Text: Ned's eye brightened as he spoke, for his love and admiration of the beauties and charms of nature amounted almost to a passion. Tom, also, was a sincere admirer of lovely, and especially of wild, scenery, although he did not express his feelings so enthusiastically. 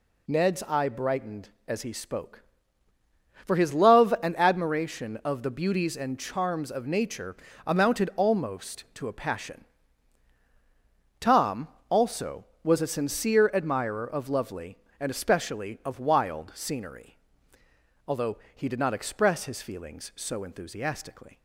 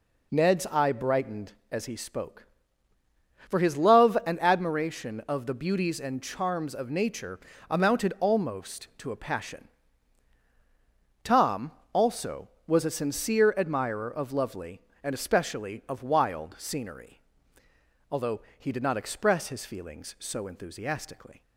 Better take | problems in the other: first | starts louder than the rest; until 1.7 s; 3.5 dB // pauses between "nature" and "amounted"; slight; at 7.3 s; 0.30 s long; slight in the first // pauses between "although" and "he"; slight; at 18.4 s; 0.16 s long; slight in the first

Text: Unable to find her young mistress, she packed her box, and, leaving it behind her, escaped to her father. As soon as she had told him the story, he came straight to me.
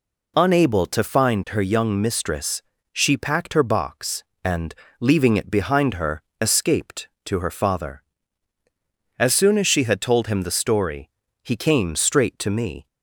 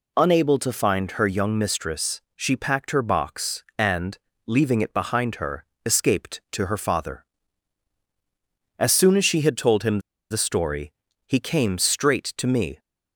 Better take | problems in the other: first | pauses between "him" and "the"; slight; at 9.9 s; 0.30 s long

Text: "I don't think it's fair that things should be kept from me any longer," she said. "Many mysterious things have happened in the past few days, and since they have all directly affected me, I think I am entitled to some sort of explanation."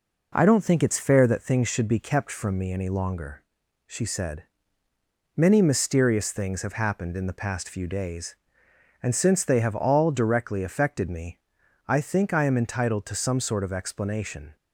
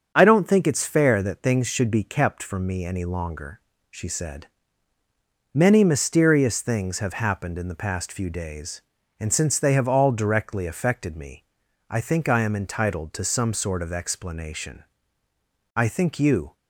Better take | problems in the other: first | starts louder than the rest; strong; until 1.1 s; 7 dB // goes on to say "I think you"; noticeable; from 15.7 s on; 0.78 s long

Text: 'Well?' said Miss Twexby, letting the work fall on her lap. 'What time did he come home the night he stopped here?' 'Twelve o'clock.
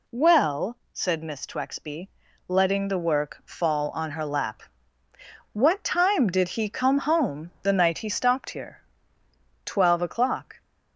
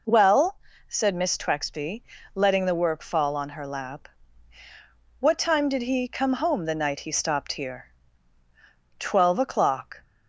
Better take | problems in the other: neither | none

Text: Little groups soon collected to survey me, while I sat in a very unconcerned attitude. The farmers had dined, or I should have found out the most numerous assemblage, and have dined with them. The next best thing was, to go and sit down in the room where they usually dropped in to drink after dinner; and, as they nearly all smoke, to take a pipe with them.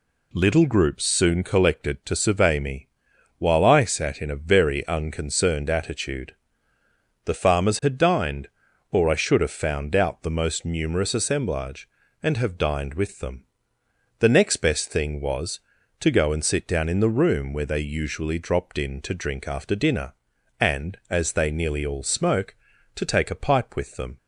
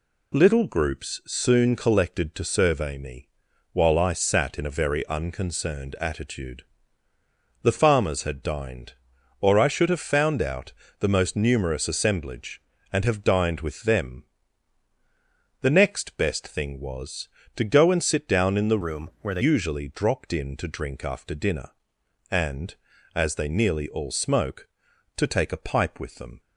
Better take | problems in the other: first | pauses between "out" and "the"; slight; at 10.7 s; 0.28 s long // changes voice from "room" to "they"; from 18.8 to 19.4 s; 0.6 s long

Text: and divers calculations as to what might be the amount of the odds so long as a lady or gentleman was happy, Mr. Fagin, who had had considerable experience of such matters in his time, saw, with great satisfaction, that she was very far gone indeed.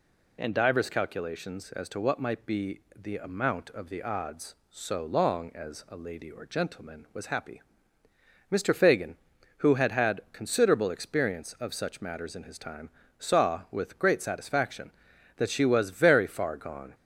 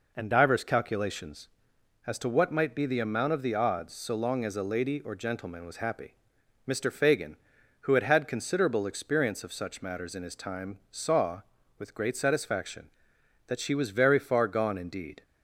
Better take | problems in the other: second | pauses between "be" and "the"; slight; at 2.7 s; 0.16 s long // stops before "indeed"; at 16.9 s

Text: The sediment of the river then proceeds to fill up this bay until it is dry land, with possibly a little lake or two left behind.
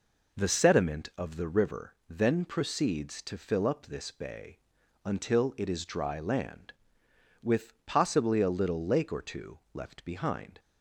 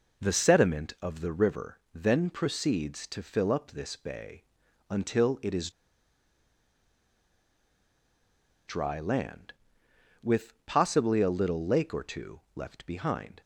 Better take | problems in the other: first | pauses between "river" and "then"; slight; at 1.7 s; 0.16 s long; slight in the first // pauses between "bay" and "until"; noticeable; at 4.4 s; 0.48 s long; noticeable in the first // pauses between "is" and "dry"; strong; at 5.6 s; 2.9 s long

